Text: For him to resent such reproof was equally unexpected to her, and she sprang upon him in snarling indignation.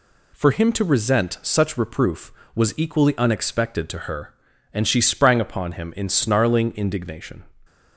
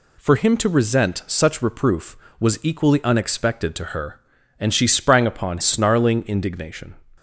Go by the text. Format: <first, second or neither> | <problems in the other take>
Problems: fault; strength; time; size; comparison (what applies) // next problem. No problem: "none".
first | skips "him in"; at 5.5 s